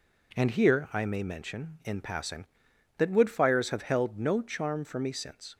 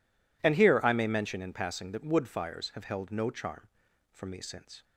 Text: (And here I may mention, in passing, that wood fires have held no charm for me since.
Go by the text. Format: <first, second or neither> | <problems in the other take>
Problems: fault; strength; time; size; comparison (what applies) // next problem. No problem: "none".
neither | none